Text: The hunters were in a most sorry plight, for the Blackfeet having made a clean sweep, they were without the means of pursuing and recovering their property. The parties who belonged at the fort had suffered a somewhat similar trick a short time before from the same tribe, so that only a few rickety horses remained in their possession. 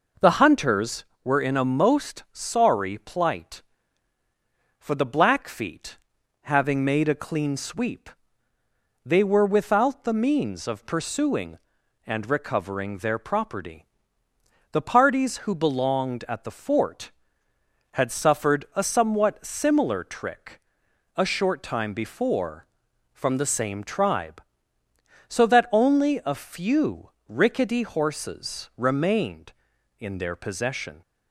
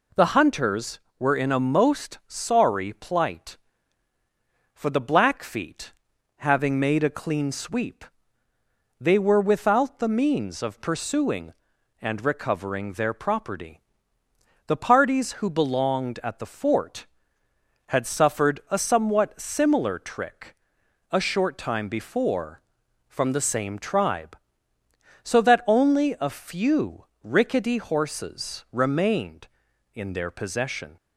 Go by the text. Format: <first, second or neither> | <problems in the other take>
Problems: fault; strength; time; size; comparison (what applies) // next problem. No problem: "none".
second | starts louder than the rest; noticeable; until 1.3 s; 5 dB // pauses between "Blackfeet" and "having"; noticeable; at 5.9 s; 0.46 s long; noticeable in the second // pauses between "trick" and "a"; noticeable; at 20.5 s; 0.56 s long; noticeable in the second // pauses between "few" and "rickety"; slight; at 27.0 s; 0.18 s long; slight in the second